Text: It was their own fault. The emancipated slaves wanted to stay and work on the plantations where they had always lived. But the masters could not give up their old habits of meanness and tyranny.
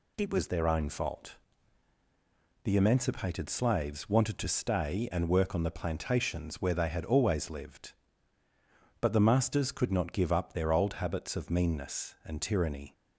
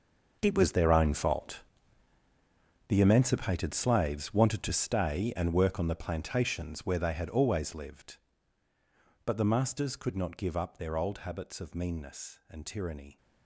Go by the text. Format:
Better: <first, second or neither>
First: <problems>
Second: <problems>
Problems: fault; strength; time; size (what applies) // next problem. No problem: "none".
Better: first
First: none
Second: gets quieter; strong; throughout; 14 dB